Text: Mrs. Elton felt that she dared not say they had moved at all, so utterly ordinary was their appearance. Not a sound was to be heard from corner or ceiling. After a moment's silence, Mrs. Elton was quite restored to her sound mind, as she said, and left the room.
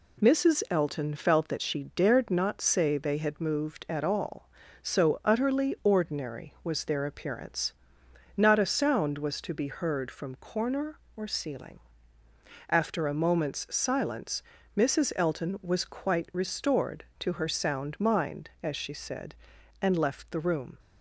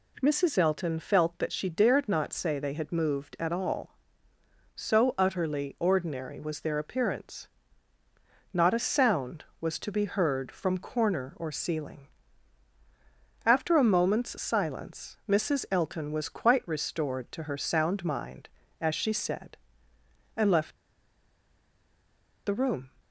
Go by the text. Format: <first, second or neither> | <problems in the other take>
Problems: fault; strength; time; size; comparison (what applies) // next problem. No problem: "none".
first | pauses between "left" and "the"; strong; at 20.7 s; 1.6 s long